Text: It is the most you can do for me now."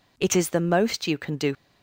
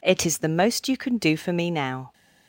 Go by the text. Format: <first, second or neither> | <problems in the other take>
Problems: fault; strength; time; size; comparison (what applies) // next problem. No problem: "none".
second | stops before "for me now"; at 1.5 s